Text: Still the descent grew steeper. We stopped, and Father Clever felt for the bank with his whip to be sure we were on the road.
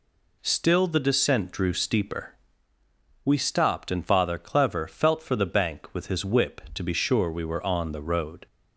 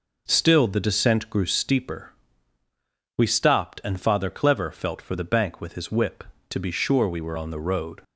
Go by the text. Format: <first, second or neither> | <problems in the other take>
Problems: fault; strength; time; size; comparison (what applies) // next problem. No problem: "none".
second | says "drew" for "grew"; at 1.5 s